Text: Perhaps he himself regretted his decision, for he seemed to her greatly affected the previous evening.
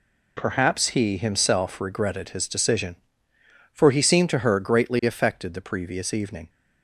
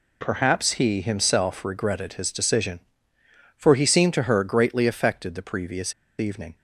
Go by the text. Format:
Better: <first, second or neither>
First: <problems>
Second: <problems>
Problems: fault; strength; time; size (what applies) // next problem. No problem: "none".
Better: first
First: none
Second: pauses between "previous" and "evening"; slight; at 5.9 s; 0.27 s long